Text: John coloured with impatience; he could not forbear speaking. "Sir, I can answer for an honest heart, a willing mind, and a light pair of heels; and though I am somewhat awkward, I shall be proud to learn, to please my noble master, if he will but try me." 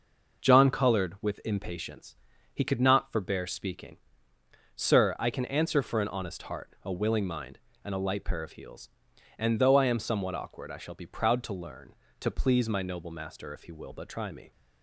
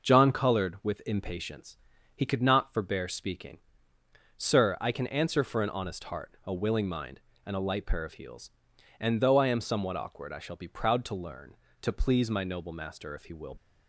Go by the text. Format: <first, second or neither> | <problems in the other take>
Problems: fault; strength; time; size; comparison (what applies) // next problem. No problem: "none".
first | stops before "but try me"; at 13.5 s